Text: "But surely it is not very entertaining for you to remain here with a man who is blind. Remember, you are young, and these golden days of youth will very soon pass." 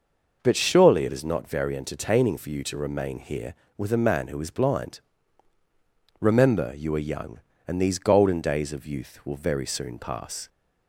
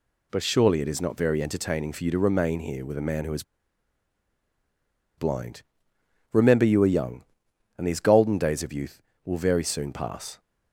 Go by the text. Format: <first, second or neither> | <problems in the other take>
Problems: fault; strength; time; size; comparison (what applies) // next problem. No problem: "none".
first | pauses between "is" and "blind"; strong; at 3.4 s; 1.7 s long